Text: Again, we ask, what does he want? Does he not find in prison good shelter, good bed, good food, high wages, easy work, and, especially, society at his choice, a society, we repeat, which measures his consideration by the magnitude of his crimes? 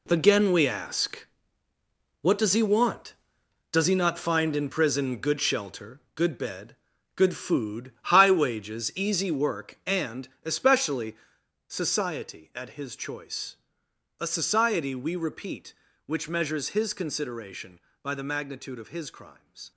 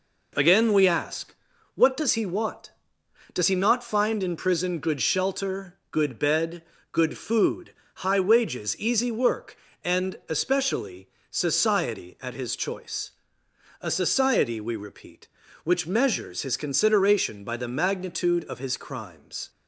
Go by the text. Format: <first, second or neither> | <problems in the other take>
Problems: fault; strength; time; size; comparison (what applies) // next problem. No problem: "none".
second | gets quieter; strong; throughout; 11.5 dB